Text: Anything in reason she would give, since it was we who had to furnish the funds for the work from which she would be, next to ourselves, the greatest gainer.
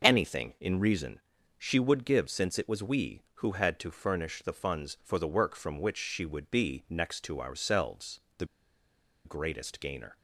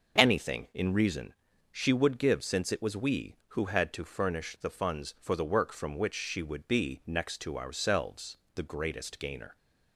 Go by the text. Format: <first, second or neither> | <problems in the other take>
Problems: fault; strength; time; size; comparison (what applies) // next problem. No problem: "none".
second | starts louder than the rest; noticeable; until 1.0 s; 6 dB; noticeable in the second // pauses between "reason" and "she"; slight; at 1.2 s; 0.36 s long; slight in the second // pauses between "the" and "greatest"; noticeable; at 8.4 s; 0.79 s long